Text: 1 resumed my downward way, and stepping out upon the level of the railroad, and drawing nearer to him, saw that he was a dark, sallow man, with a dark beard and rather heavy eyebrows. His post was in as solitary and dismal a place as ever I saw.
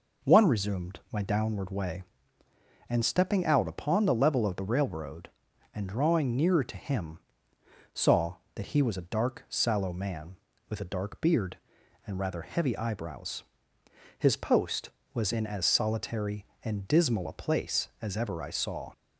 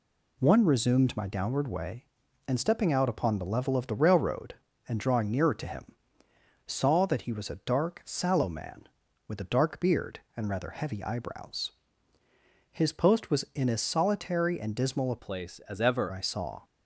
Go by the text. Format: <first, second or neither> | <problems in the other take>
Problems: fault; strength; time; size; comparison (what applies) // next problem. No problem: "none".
first | changes voice from "place" to "ever"; from 15.1 to 16.1 s; 1.0 s long